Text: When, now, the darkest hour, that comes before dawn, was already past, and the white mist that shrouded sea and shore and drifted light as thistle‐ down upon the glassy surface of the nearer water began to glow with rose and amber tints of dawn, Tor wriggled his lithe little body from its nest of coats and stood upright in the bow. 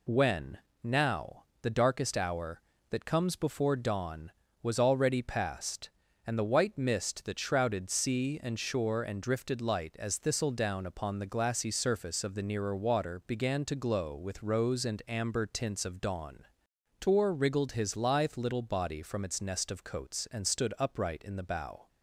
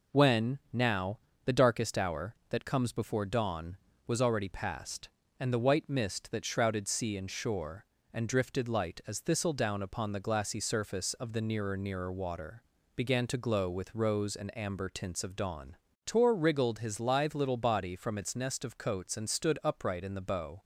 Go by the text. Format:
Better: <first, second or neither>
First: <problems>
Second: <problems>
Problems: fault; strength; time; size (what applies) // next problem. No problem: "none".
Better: first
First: none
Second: says "nearer" twice; at 11.7 s // pauses between "water" and "began"; slight; at 12.6 s; 0.34 s long